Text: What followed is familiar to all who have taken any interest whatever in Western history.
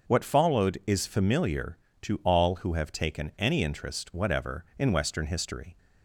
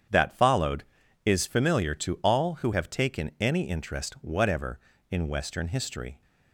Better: first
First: starts louder than the rest; noticeable; until 1.1 s; 6 dB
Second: starts louder than the rest; strong; until 1.5 s; 8.5 dB // says "That" for "What"; at 0.0 s

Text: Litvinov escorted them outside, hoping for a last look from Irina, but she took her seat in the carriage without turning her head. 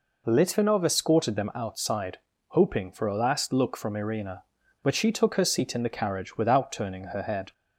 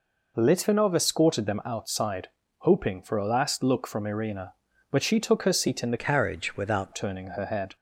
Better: first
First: none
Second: changes voice from "carriage" to "without"; from 5.9 to 6.9 s; 1.0 s long

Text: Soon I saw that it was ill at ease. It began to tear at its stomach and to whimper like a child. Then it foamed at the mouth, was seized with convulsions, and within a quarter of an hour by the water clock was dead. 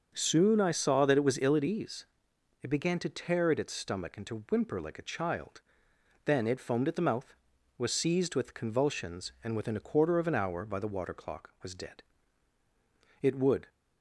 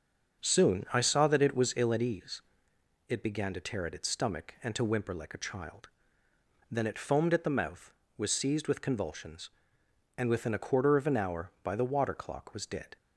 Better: second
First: starts louder than the rest; until 1.1 s; 6 dB // goes on to say "It would"; slight; from 13.2 s on; 0.44 s long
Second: starts louder than the rest; until 1.4 s; 7 dB

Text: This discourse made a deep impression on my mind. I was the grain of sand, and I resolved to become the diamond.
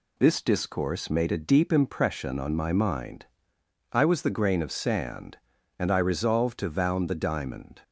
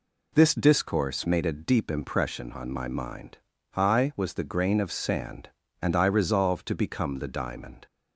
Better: second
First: says "vound" for "become"; at 6.6 s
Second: none

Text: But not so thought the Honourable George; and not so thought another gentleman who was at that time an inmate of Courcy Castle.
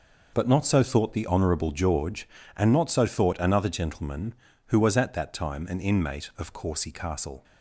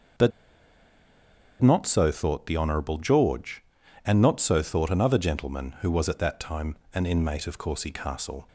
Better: first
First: none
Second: starts louder than the rest; noticeable; until 2.5 s; 6 dB // pauses between "But" and "not"; strong; at 0.3 s; 1.3 s long // pauses between "time" and "an"; slight; at 6.7 s; 0.20 s long

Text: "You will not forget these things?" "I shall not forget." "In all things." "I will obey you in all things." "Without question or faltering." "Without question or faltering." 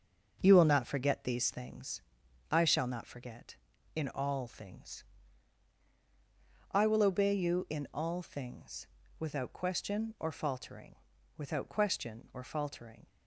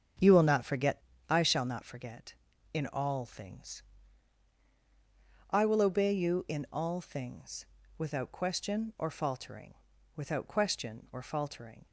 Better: first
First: starts louder than the rest; until 1.4 s; 7 dB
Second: starts louder than the rest; strong; until 1.4 s; 7 dB // skips "these things"; at 1.1 s

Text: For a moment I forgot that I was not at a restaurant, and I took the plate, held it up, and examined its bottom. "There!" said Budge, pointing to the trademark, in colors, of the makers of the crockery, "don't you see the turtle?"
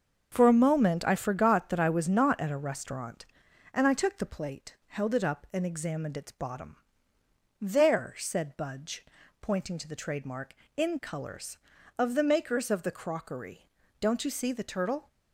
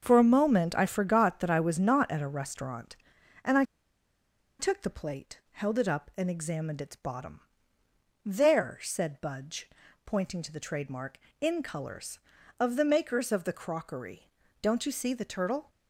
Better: first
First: starts louder than the rest; until 1.3 s; 6 dB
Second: starts louder than the rest; until 1.0 s; 6 dB // pauses between "I" and "took"; noticeable; at 3.6 s; 0.95 s long

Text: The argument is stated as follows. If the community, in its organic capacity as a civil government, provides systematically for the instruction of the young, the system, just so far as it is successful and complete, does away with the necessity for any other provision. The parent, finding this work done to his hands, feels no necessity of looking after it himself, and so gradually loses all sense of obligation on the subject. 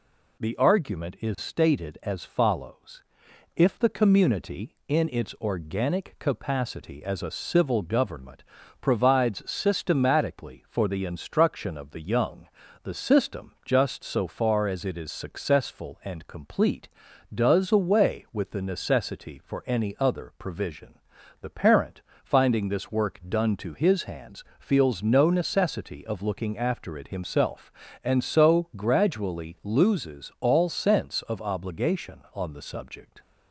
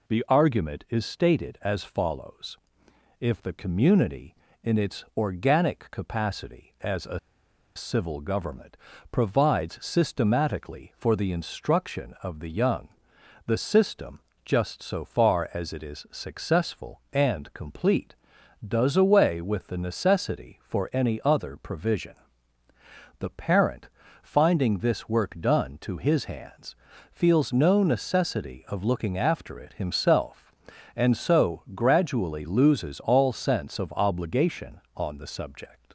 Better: first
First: none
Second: pauses between "a" and "civil"; noticeable; at 7.1 s; 0.57 s long

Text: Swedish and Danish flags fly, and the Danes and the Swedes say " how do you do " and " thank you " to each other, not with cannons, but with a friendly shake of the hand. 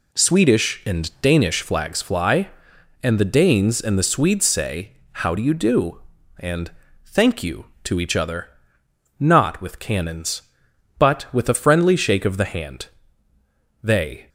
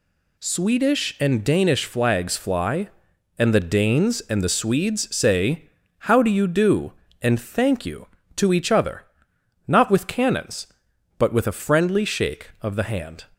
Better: second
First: goes on to say "They"; slight; from 13.8 s on; 0.46 s long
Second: none

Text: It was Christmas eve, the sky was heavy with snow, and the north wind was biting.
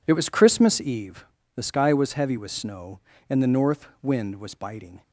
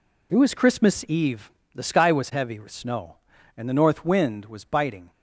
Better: neither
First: none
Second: none

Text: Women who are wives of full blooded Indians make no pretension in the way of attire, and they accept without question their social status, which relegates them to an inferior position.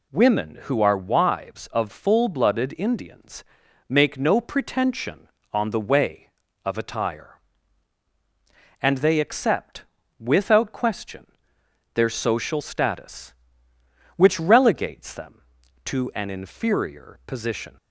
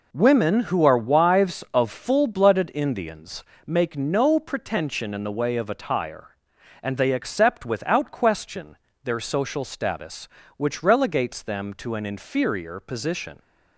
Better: second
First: pauses between "Indians" and "make"; noticeable; at 3.4 s; 0.46 s long // says "on" for "in"; at 5.5 s // pauses between "accept" and "without"; slight; at 9.8 s; 0.36 s long // pauses between "question" and "their"; noticeable; at 11.2 s; 0.66 s long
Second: pauses between "Indians" and "make"; slight; at 3.4 s; 0.20 s long // pauses between "question" and "their"; slight; at 8.7 s; 0.28 s long

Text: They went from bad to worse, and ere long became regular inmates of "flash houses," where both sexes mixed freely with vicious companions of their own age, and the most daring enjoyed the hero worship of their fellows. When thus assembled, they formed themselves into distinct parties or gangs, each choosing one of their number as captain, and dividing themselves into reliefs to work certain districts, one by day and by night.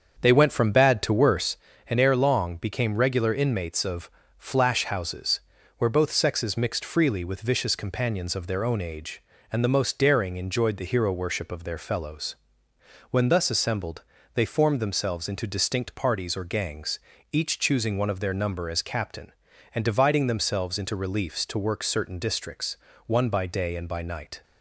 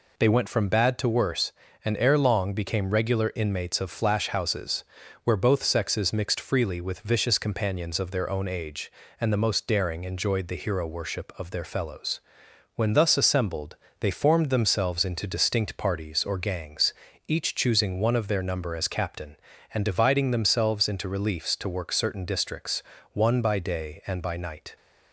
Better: second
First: starts louder than the rest; strong; until 1.6 s; 7 dB // pauses between "of" and "flash"; slight; at 4.0 s; 0.26 s long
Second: none

